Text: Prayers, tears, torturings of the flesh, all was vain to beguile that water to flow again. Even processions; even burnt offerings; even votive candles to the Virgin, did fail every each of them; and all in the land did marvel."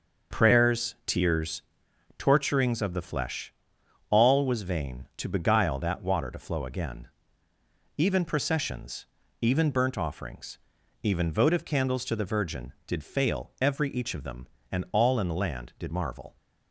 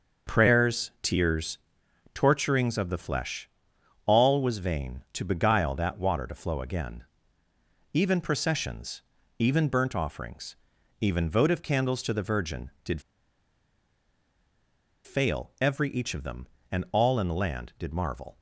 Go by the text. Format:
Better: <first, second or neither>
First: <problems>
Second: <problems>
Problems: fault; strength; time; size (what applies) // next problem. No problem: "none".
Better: first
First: none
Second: pauses between "did" and "fail"; strong; at 12.9 s; 2.0 s long